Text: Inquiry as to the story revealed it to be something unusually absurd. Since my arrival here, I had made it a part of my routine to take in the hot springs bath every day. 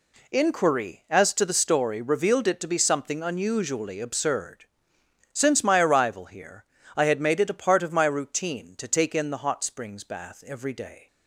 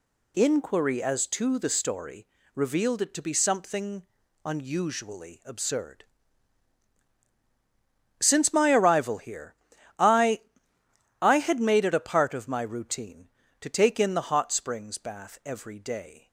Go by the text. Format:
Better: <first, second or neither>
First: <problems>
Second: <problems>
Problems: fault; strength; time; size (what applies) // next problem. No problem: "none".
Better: first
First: none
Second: pauses between "story" and "revealed"; slight; at 2.2 s; 0.28 s long // pauses between "something" and "unusually"; at 4.0 s; 0.40 s long // says "I" twice; at 11.2 s